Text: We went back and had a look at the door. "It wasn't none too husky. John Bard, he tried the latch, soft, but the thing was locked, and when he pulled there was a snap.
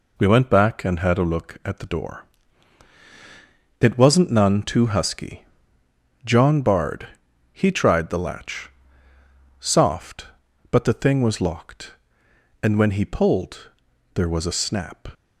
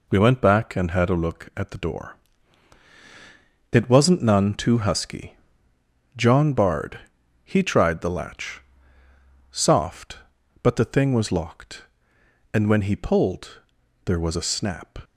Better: neither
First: pauses between "pulled" and "there"; noticeable; at 13.6 s; 0.46 s long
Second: pauses between "pulled" and "there"; noticeable; at 13.5 s; 0.46 s long

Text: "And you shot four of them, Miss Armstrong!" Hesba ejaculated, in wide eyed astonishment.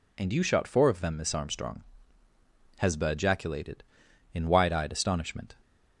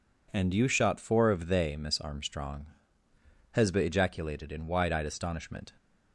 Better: first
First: none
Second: says "they" for "them"; at 1.4 s

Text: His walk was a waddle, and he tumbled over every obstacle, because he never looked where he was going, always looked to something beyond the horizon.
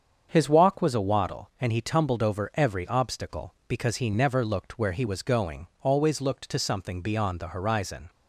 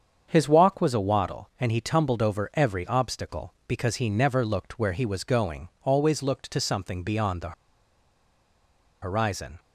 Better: first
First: starts louder than the rest; strong; until 1.3 s; 7.5 dB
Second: starts louder than the rest; strong; until 1.3 s; 7.5 dB // pauses between "the" and "horizon"; strong; at 7.5 s; 1.5 s long

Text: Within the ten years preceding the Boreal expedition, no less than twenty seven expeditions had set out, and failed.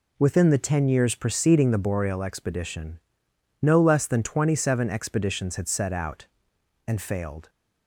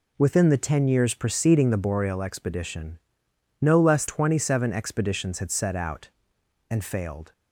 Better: first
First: none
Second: skips "than"; at 4.0 s

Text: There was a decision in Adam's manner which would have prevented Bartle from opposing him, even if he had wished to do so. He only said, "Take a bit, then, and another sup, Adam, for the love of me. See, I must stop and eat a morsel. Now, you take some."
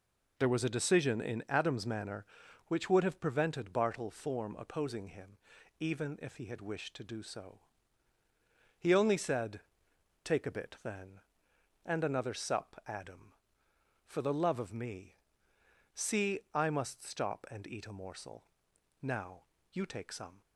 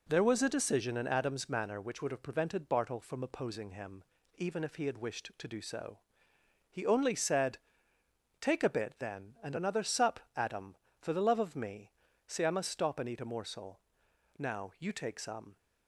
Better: second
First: says "form" for "from"; at 4.1 s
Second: none

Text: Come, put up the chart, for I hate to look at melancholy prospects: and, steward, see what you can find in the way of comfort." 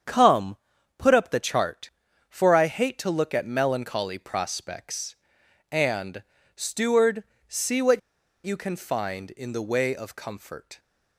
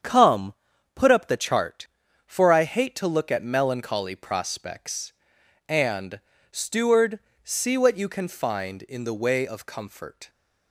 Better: second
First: starts louder than the rest; strong; until 1.4 s; 8 dB // pauses between "what" and "you"; at 7.9 s; 0.44 s long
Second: starts louder than the rest; strong; until 1.4 s; 8 dB

